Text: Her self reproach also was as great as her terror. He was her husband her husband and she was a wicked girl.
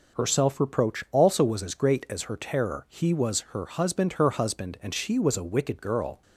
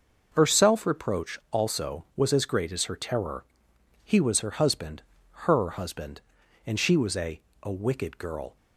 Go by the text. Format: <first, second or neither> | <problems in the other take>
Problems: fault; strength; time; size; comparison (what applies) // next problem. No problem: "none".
first | pauses between "husband" and "her"; at 5.0 s; 0.44 s long // says "a" twice; at 7.6 s